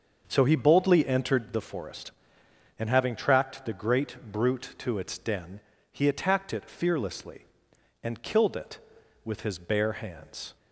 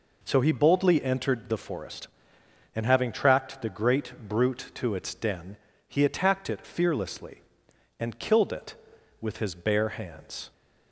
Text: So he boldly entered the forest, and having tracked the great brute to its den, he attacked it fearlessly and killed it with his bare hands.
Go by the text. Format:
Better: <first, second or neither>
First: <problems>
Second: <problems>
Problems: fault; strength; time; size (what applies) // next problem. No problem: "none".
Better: second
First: starts louder than the rest; until 1.5 s; 6.5 dB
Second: none